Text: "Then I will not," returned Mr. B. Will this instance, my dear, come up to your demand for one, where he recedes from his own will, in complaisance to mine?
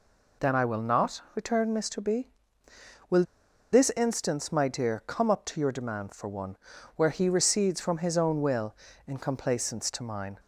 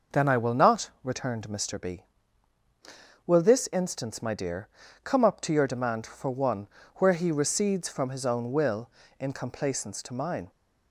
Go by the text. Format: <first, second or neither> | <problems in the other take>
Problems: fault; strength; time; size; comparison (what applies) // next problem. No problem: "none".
second | pauses between "Will" and "this"; noticeable; at 3.2 s; 0.49 s long